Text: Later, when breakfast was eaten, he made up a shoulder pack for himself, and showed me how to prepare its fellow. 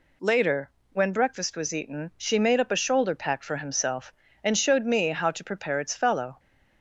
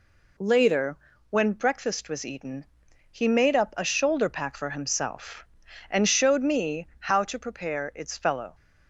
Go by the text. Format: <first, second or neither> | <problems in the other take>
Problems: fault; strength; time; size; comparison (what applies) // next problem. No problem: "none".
second | says "she" for "he"; at 2.1 s